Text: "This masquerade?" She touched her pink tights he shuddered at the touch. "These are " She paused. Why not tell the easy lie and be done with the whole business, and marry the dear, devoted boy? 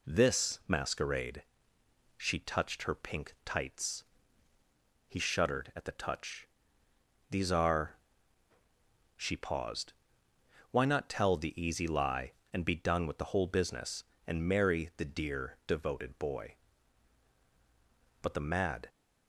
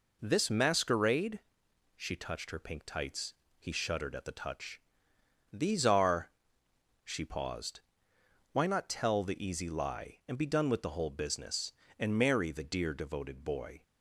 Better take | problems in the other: second | pauses between "tights" and "he"; at 4.0 s; 1.0 s long; slight in the second // goes on to say "But the mad"; noticeable; from 18.2 s on; 0.66 s long

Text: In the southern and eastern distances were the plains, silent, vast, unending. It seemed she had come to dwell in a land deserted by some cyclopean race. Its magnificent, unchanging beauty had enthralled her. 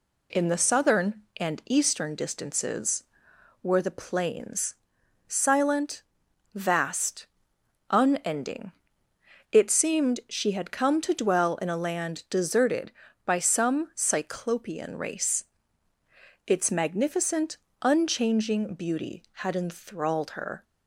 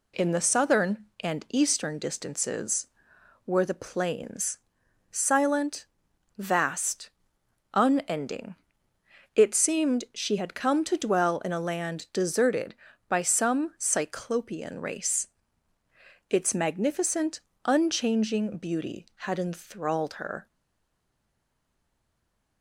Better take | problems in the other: first | stays silent after the last word; from 20.4 s on; 2.2 s long

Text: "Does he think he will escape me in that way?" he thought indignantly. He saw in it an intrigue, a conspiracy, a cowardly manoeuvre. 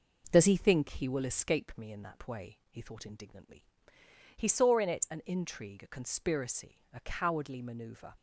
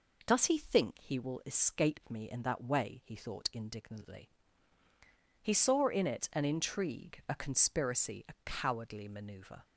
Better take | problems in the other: neither | none

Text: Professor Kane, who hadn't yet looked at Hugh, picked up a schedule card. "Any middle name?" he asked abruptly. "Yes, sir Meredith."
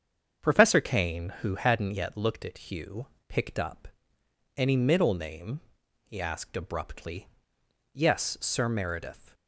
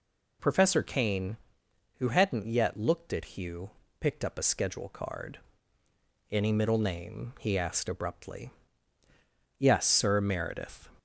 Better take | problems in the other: second | starts louder than the rest; strong; until 1.5 s; 7.5 dB // skips "a schedule card"; at 4.2 s

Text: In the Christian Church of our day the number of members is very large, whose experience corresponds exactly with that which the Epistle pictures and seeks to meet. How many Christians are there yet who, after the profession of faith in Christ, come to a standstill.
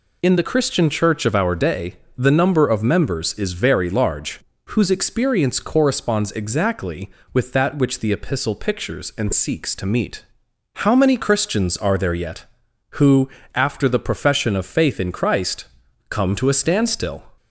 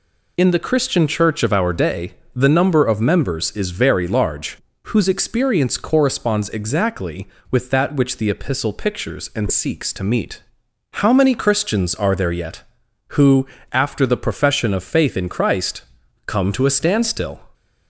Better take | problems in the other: neither | pauses between "day" and "the"; slight; the same in both

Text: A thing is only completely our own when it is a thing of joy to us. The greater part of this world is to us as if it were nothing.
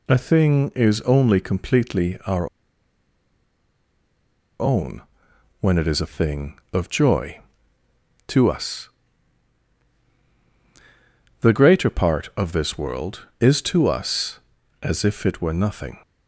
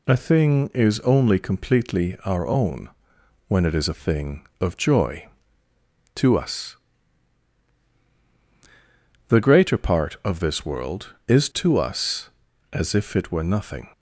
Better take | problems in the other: second | pauses between "our" and "own"; strong; at 2.4 s; 2.1 s long // pauses between "own" and "when"; noticeable; at 5.0 s; 0.60 s long; noticeable in the second

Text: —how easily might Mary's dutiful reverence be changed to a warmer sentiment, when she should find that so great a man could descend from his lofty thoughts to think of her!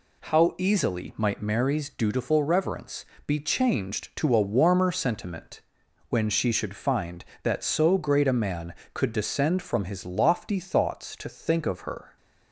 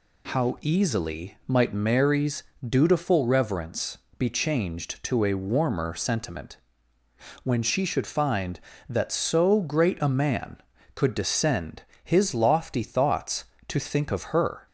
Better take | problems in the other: first | pauses between "Mary's" and "dutiful"; slight; at 2.4 s; 0.26 s long // pauses between "reverence" and "be"; slight; at 3.9 s; 0.20 s long; slight in the first // skips "from"; at 11.9 s

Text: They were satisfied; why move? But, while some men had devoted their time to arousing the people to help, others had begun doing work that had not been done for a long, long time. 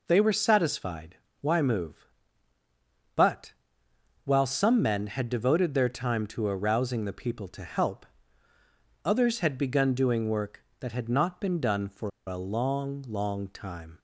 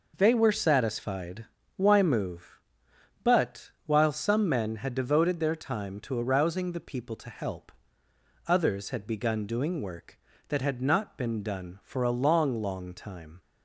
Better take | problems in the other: second | pauses between "for" and "a"; slight; at 12.0 s; 0.16 s long

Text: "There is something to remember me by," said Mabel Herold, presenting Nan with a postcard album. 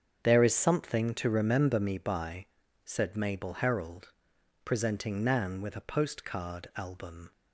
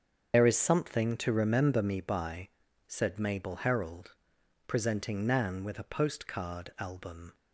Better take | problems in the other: first | loses the start of "There"; at 0.3 s; 80 ms // starts louder than the rest; until 1.3 s; 7 dB; strong in the first

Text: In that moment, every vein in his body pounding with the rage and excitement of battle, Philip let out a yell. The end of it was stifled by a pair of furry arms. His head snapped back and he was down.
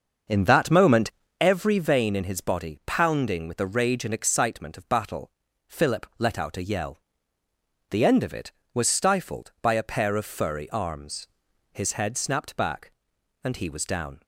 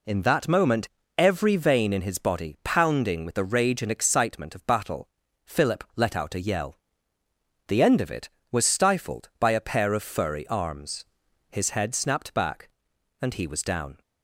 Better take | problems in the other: second | starts louder than the rest; until 1.5 s; 6.5 dB

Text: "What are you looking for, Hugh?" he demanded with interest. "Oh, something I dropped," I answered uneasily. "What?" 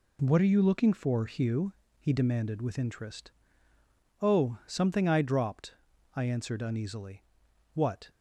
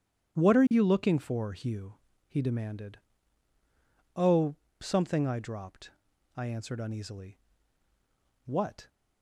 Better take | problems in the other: first | starts louder than the rest; strong; until 1.4 s; 10 dB // skips "with interest"; at 3.5 s

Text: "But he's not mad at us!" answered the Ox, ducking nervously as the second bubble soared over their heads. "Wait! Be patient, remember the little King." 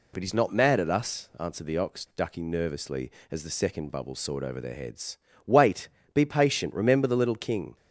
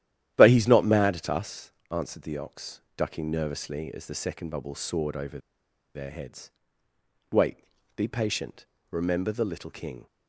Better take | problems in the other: first | starts louder than the rest; strong; until 1.3 s; 11.5 dB // pauses between "over" and "their"; noticeable; at 5.3 s; 0.57 s long

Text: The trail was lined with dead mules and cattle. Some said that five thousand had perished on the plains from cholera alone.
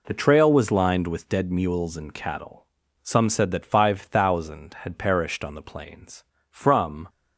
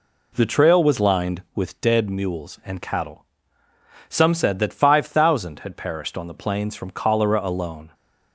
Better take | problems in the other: second | stops before "cholera alone"; at 7.0 s

